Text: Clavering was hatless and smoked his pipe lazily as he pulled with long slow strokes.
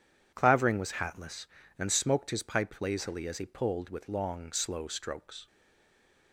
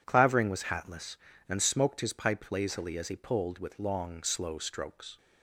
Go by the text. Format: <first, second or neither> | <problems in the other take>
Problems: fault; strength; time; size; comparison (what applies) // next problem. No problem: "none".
second | stays silent after the last word; slight; from 5.4 s on; 0.9 s long